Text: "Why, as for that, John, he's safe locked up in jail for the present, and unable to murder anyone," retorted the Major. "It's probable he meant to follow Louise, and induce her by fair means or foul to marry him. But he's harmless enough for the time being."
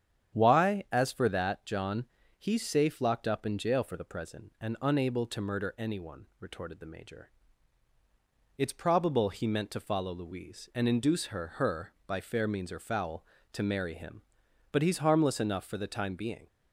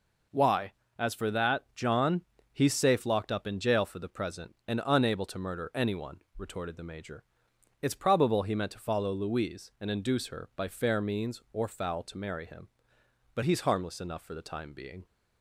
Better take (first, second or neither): second